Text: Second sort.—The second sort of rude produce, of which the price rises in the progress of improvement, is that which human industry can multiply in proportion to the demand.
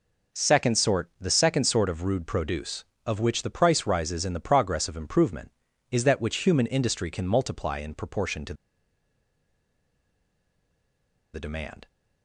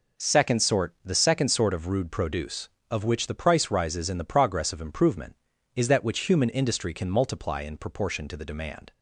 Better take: second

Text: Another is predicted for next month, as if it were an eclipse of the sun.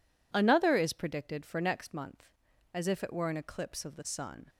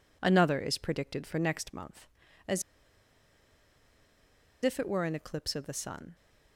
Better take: first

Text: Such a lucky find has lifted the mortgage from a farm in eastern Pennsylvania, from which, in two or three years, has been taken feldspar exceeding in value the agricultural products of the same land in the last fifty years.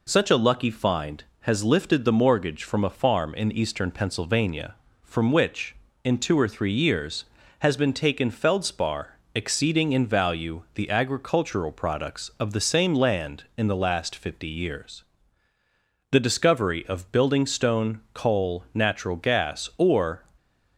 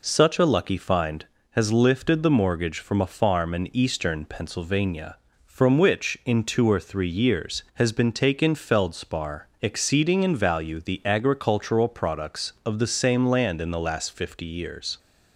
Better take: second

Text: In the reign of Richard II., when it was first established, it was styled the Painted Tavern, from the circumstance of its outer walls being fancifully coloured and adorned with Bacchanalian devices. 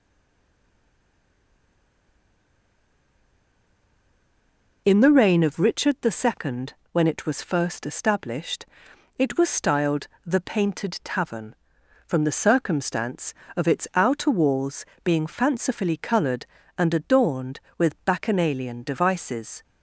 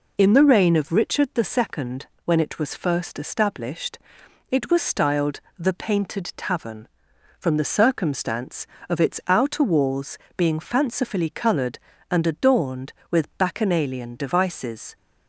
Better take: second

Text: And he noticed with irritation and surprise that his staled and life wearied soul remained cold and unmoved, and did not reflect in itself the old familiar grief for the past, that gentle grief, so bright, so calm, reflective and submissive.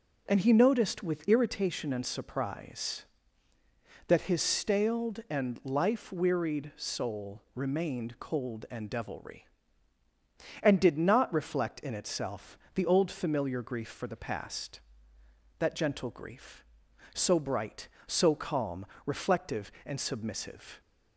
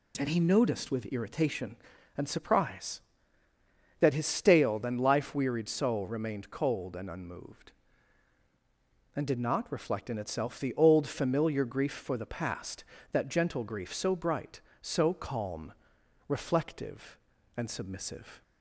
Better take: second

